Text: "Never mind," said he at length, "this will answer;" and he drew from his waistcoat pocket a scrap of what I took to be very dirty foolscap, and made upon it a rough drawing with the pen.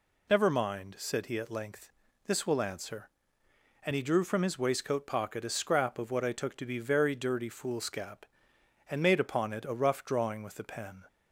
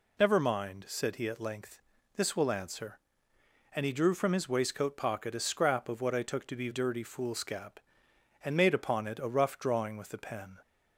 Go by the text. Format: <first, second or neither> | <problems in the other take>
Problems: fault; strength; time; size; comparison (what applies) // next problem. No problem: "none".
first | skips "very"; at 6.6 s